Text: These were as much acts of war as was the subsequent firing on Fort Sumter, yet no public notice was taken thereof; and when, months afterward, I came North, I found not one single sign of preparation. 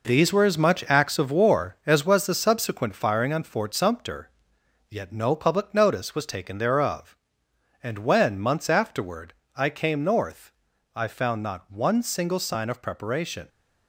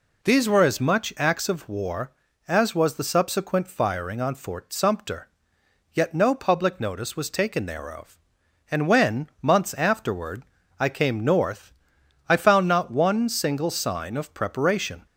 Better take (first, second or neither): second